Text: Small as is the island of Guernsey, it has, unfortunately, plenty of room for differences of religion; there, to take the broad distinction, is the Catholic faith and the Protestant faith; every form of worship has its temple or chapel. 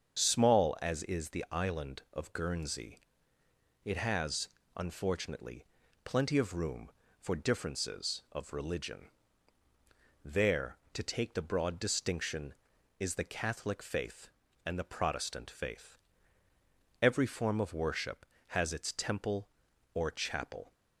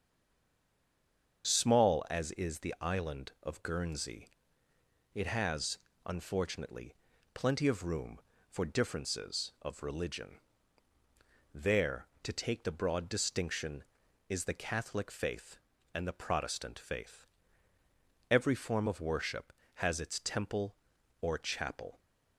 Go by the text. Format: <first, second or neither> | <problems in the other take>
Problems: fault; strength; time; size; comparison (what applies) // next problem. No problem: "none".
first | stays silent before the first word; noticeable; until 1.4 s; 1.4 s long // starts louder than the rest; until 2.5 s; 7 dB; also in the first